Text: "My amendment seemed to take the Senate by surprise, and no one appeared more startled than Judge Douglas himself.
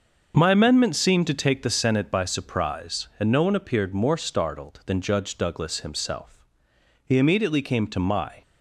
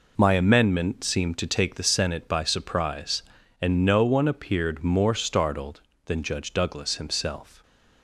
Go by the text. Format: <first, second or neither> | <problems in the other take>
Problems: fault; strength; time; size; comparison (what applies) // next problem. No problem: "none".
second | starts louder than the rest; until 1.3 s; 6.5 dB // goes on to say "He immediately came to my"; from 7.0 s on; 1.3 s long